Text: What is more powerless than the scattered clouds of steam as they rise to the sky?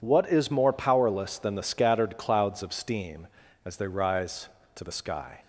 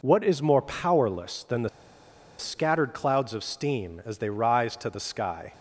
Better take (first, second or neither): first